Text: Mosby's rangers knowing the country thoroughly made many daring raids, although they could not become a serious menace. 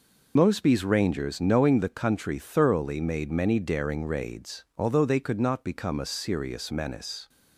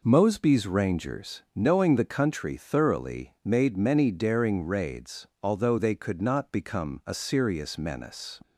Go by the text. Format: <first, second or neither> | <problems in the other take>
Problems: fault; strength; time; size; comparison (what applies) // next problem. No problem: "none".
second | loses the start of "Mosby's"; at 0.3 s; 55 ms